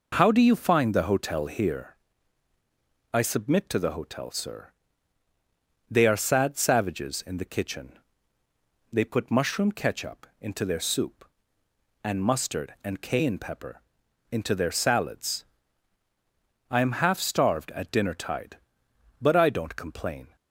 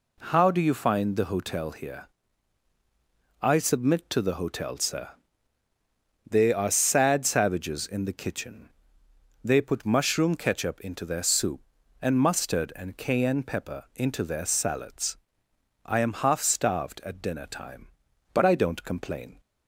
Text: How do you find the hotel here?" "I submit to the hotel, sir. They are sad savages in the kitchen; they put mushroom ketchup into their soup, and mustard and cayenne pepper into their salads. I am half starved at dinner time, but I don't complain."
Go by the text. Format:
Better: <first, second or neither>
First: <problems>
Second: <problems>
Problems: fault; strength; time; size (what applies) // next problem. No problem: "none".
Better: second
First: pauses between "pepper" and "into"; noticeable; at 13.8 s; 0.48 s long // says "tide" for "time"; at 18.1 s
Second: none